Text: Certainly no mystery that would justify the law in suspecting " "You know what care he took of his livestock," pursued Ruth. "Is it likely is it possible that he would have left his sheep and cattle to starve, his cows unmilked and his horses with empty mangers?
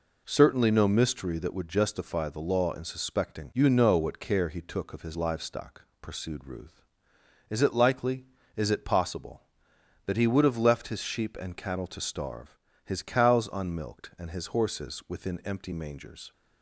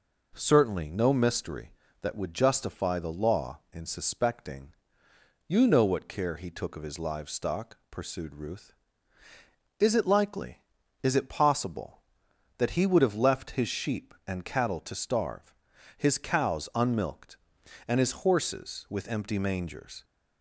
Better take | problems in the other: second | says "within" for "with"; at 15.0 s

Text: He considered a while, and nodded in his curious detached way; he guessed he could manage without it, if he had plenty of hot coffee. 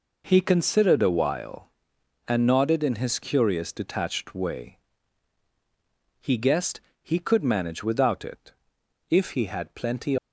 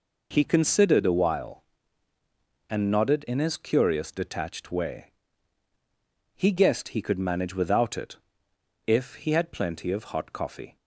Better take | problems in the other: second | pauses between "guessed" and "he"; slight; at 6.8 s; 0.22 s long // stops before "of hot coffee"; at 10.1 s

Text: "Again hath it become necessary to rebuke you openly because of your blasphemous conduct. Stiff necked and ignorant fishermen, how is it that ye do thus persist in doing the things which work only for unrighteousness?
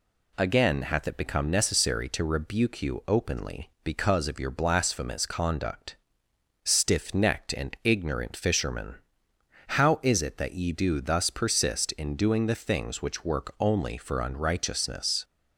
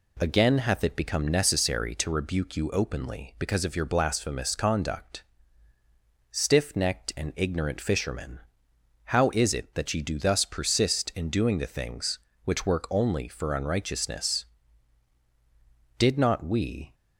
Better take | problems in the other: first | goes on to say "Did not we"; noticeable; from 15.9 s on; 0.96 s long

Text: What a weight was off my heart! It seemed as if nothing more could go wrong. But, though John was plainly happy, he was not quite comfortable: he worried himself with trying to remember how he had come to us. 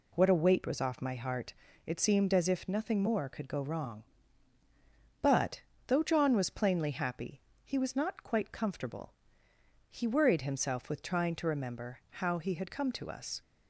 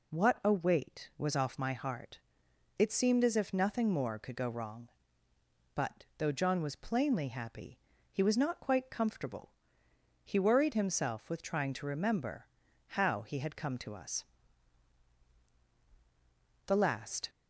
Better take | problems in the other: first | pauses between "remember" and "how"; noticeable; at 12.4 s; 0.46 s long // goes on to say "The last"; noticeable; from 16.6 s on; 0.64 s long

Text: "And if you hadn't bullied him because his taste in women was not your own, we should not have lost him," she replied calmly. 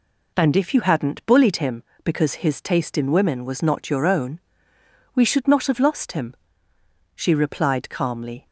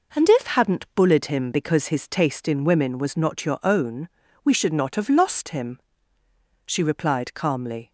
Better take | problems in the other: first | skips "you"; at 0.4 s

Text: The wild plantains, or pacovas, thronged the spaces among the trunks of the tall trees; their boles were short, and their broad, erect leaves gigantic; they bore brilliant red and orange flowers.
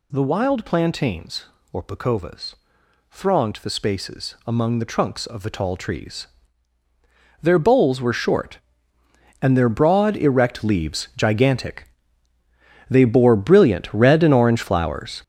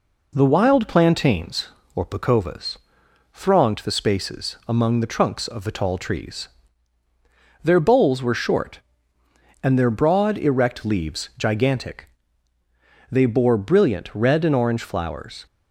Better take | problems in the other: second | gets louder; strong; throughout; 9 dB

